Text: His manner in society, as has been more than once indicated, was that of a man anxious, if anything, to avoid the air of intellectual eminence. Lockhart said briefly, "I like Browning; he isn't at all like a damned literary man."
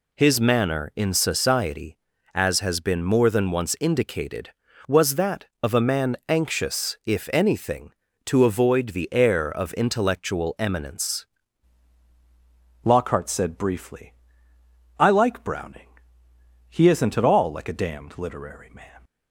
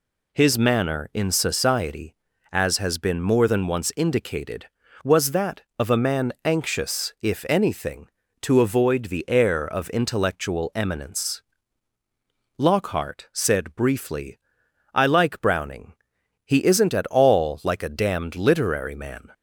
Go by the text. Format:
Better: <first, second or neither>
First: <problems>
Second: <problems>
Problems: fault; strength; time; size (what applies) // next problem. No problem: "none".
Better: second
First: changes voice at "Lockhart"; from 12.8 s on; 6.2 s long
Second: none